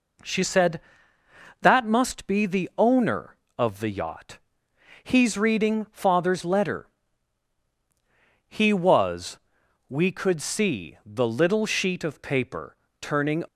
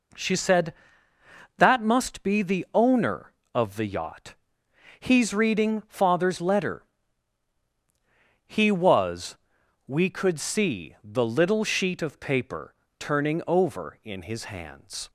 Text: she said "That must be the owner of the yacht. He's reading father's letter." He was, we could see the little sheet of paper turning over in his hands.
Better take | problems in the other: second | pauses between "paper" and "turning"; slight; at 12.7 s; 0.26 s long; slight in the second // stops before "over in his hands"; at 13.4 s

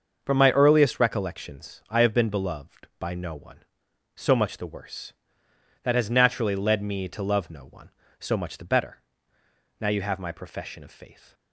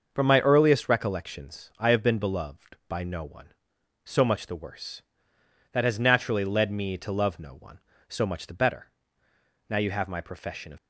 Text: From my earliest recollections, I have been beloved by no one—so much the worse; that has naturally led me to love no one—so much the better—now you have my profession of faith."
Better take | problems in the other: first | starts louder than the rest; until 1.1 s; 6.5 dB; also in the first // stops before "faith"; at 10.7 s

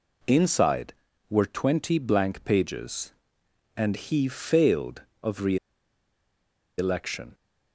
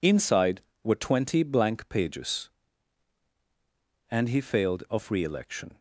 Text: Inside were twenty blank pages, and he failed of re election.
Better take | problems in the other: second | pauses between "re" and "election"; at 5.5 s; 1.2 s long

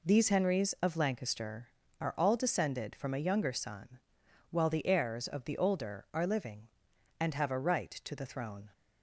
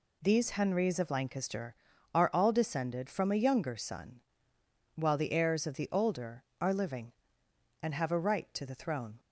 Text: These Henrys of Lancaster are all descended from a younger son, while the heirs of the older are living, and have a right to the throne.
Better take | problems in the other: neither | none

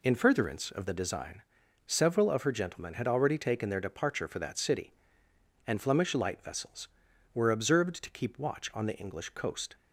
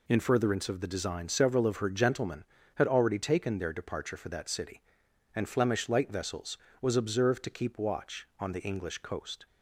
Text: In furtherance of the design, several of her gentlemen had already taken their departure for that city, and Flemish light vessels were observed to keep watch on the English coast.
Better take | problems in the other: first | says "was" for "were"; at 6.7 s

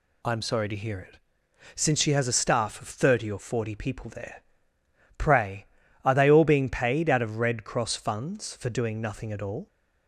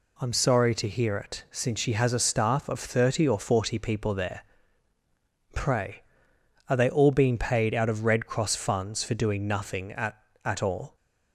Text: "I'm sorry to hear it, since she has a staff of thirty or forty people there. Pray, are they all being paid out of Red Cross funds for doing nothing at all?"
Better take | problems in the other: first | says "at" twice; at 10.4 s

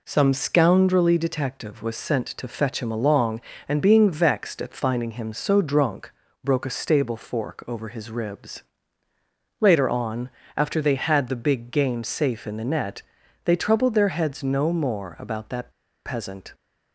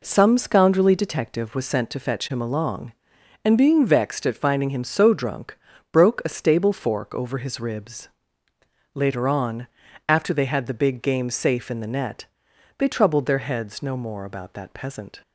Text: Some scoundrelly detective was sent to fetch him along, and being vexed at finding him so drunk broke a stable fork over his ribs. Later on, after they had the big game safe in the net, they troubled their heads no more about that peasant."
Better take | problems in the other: second | pauses between "drunk" and "broke"; slight; at 6.1 s; 0.32 s long; also in the second // pauses between "that" and "peasant"; at 15.6 s; 0.36 s long

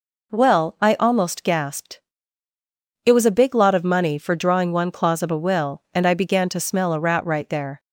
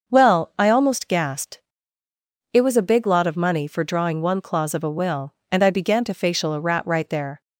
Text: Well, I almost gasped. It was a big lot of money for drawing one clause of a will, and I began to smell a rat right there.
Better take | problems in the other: first | starts louder than the rest; until 1.1 s; 6.5 dB // says "facial" for "smell"; at 6.1 s

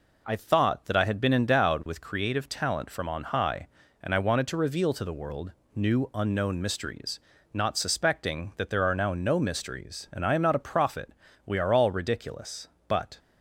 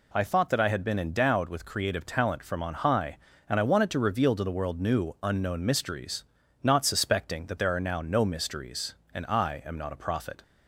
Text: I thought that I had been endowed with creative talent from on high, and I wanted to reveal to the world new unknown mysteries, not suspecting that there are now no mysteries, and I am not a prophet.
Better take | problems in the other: second | pauses between "world" and "new"; slight; at 5.5 s; 0.20 s long // goes on to say "We are all ridiculous but"; strong; from 11.4 s on; 1.7 s long

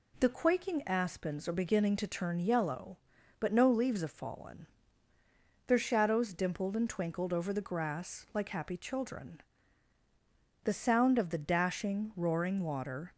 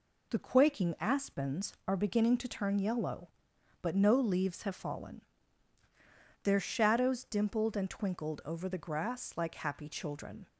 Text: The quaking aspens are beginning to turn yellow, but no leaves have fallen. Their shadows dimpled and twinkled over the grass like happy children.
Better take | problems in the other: second | goes on to say "The sound of the dashing roaring water"; strong; from 10.6 s on; 2.5 s long

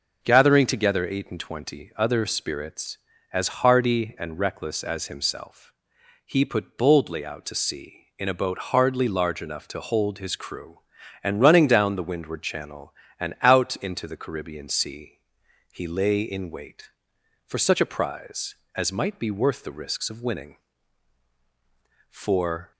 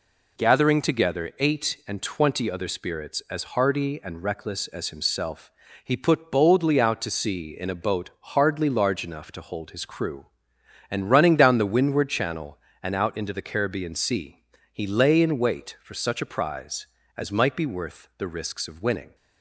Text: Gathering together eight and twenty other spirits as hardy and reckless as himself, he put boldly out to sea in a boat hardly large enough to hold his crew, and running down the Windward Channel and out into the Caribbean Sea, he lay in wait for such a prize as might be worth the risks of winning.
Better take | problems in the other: second | goes on to say "For"; noticeable; from 22.0 s on; 0.62 s long

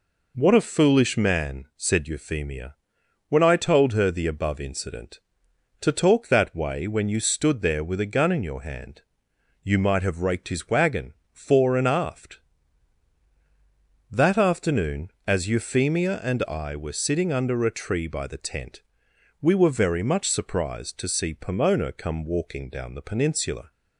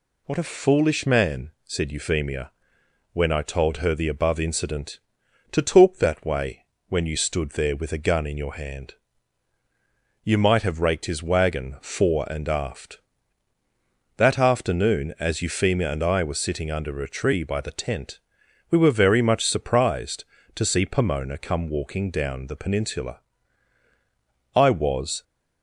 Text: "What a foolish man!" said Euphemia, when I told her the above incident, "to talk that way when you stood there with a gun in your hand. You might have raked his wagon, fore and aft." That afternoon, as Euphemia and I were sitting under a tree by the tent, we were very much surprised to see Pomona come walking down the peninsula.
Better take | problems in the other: first | pauses between "way" and "when"; slight; at 6.6 s; 0.24 s long // goes on to say "I was"; noticeable; from 24.5 s on; 0.68 s long

